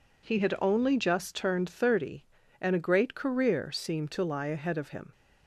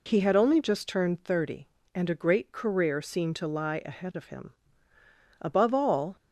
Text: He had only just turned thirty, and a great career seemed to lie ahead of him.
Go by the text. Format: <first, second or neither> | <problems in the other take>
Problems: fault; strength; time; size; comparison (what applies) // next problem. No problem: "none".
first | goes on to say "Above all"; noticeable; from 5.3 s on; 0.76 s long